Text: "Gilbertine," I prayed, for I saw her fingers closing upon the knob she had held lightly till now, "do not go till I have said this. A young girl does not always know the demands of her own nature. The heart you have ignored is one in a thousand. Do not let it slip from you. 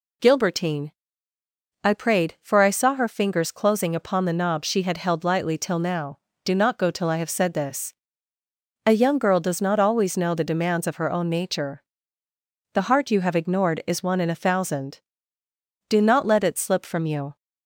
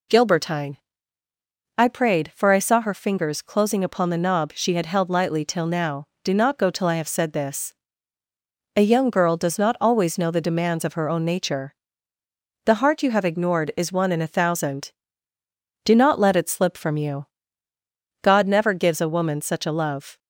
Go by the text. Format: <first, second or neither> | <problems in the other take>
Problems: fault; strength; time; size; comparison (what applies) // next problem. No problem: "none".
first | goes on to say "God never gives a woman such a love"; strong; from 18.2 s on; 1.9 s long